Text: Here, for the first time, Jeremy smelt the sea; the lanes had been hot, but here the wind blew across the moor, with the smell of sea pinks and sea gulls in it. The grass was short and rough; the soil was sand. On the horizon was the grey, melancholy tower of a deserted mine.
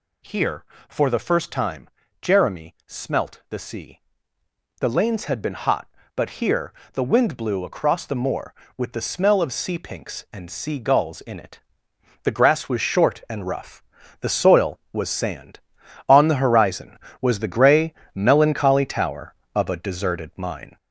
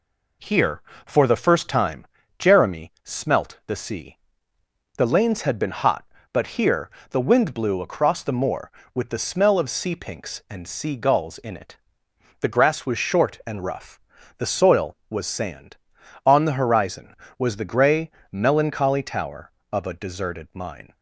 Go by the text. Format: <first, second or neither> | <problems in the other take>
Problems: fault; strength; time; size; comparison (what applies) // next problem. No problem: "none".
second | gets louder; noticeable; throughout; 5.5 dB // pauses between "here" and "the"; slight; at 6.7 s; 0.20 s long; slight in the second